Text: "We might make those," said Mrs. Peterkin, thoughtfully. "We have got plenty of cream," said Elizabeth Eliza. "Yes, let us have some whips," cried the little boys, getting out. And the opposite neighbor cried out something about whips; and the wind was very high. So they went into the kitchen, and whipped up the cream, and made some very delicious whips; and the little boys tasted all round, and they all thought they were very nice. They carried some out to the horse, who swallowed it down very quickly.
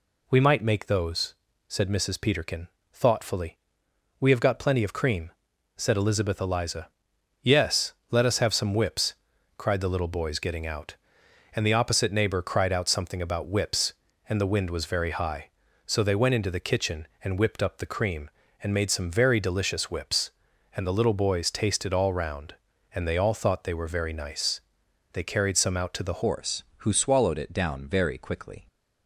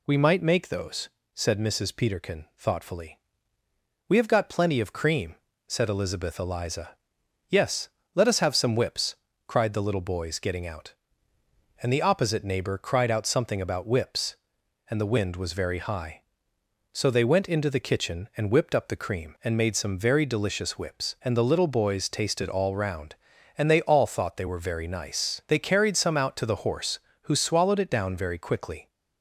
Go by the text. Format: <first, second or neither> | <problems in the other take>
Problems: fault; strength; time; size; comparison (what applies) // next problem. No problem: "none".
second | changes voice at "horse"; from 26.2 s on; 2.4 s long